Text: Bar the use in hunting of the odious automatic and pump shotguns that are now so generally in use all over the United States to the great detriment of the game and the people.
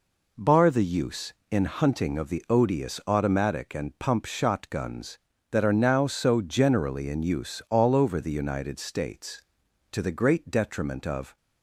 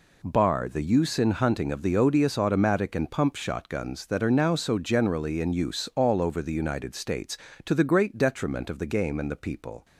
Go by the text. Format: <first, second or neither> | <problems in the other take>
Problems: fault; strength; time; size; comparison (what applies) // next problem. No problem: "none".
second | stops before "the game and the people"; at 11.3 s